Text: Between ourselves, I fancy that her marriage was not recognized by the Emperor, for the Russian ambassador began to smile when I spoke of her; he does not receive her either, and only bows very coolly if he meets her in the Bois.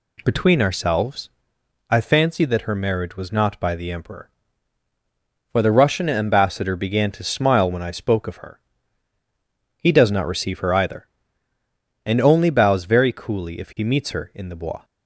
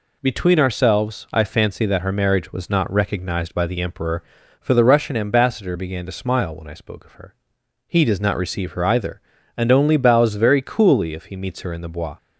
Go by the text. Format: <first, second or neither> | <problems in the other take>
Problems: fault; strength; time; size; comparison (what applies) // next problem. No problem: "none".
second | skips "recognized"; at 3.5 s